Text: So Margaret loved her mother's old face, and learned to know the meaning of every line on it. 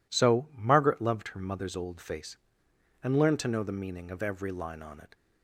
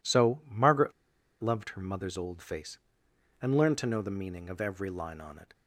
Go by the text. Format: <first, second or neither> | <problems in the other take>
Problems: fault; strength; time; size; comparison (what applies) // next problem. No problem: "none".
first | pauses between "Margaret" and "loved"; noticeable; at 0.9 s; 0.50 s long